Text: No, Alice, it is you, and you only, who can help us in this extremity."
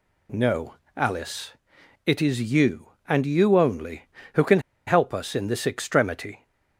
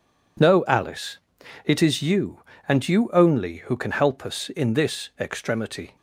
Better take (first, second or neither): second